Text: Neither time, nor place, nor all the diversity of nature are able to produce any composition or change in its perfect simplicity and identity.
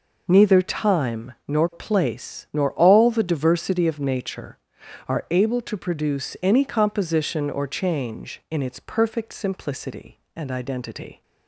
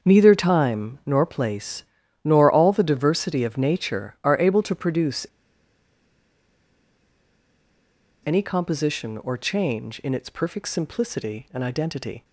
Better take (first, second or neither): first